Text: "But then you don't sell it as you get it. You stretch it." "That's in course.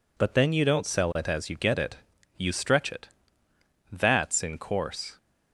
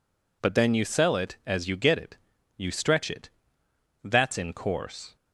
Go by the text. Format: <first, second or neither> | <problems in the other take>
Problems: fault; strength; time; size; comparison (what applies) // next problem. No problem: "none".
first | skips "don't"; at 0.8 s